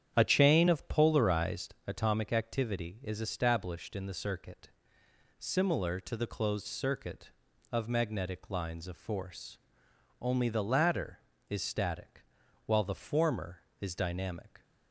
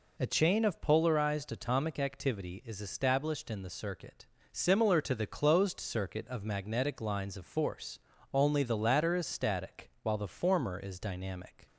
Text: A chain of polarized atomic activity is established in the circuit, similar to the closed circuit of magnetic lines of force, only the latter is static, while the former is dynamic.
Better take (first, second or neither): second